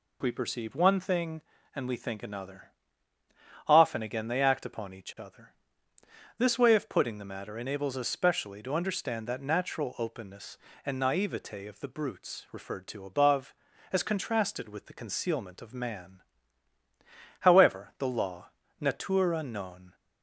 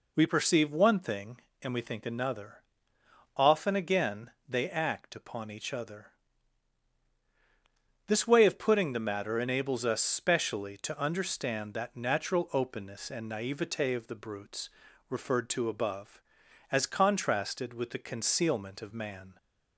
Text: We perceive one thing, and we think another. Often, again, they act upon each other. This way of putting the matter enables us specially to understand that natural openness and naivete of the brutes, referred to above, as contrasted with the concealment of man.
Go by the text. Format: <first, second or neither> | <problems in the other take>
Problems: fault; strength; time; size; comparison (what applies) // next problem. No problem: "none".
second | goes on to say "However the law natura non"; strong; from 17.4 s on; 2.5 s long